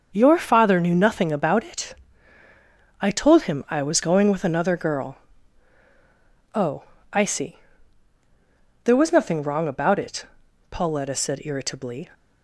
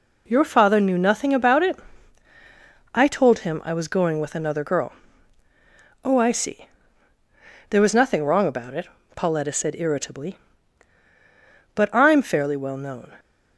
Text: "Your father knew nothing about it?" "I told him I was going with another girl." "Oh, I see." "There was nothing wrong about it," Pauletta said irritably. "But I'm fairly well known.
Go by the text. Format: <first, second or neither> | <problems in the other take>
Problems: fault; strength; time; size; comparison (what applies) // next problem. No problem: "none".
second | starts louder than the rest; until 1.1 s; 6.5 dB // stops before "But I'm fairly well known"; at 12.1 s